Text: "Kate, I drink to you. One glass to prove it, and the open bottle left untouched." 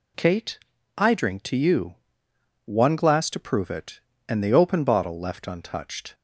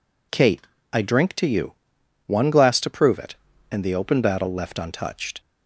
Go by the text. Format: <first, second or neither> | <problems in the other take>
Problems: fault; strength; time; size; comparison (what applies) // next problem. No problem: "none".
first | says "battle" for "bottle"; at 4.2 s